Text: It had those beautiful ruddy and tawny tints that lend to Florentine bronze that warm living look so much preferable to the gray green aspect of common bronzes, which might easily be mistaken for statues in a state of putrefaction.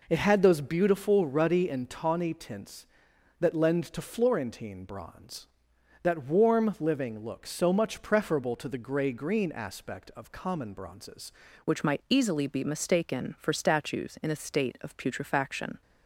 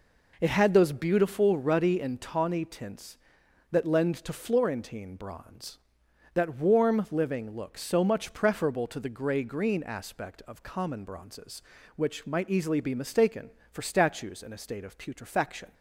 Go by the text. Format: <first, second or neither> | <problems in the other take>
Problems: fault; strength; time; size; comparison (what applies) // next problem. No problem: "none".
second | changes voice at "which"; from 11.6 s on; 4.2 s long